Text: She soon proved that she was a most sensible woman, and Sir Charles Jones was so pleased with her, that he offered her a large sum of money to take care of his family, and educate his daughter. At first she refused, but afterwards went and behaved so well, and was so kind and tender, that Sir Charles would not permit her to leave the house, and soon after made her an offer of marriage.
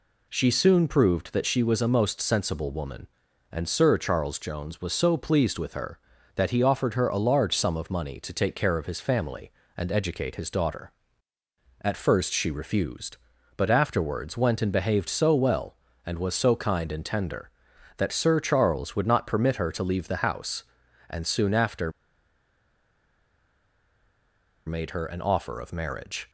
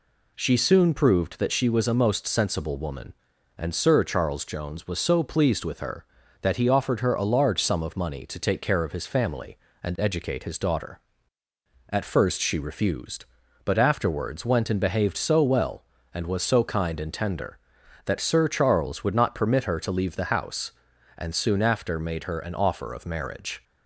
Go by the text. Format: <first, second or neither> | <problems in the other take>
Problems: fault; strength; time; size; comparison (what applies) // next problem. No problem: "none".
second | pauses between "after" and "made"; strong; at 21.8 s; 2.7 s long